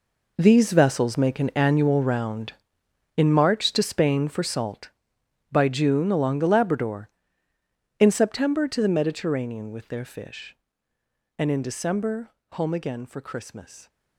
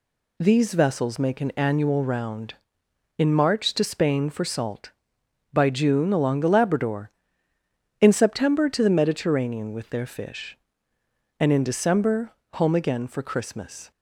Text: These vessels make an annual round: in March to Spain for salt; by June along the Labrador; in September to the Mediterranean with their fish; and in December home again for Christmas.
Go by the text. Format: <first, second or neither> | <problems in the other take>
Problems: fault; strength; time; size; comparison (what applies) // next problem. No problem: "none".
second | gets quieter; strong; throughout; 14 dB // pauses between "December" and "home"; slight; at 12.3 s; 0.20 s long; slight in the second